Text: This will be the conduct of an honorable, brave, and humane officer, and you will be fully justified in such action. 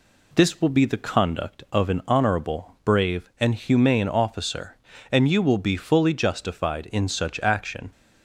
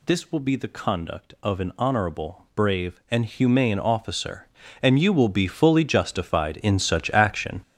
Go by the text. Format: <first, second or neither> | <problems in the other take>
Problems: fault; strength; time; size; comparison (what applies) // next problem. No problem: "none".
first | gets louder; strong; throughout; 10.5 dB